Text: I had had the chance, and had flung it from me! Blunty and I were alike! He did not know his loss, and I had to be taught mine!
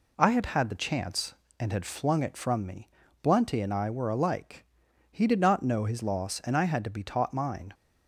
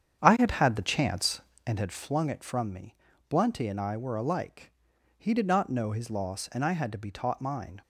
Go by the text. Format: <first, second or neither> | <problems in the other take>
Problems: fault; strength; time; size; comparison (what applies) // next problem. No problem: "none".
first | starts louder than the rest; strong; until 1.9 s; 8.5 dB